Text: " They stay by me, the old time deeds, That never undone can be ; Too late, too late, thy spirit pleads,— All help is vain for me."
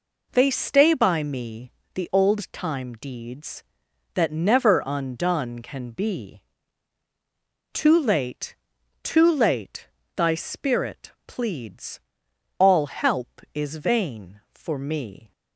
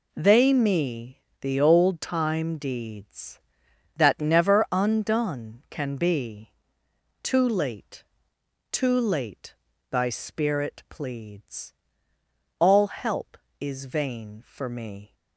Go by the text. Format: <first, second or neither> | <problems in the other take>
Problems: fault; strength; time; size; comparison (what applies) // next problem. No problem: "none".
first | skips "stay by"; at 0.5 s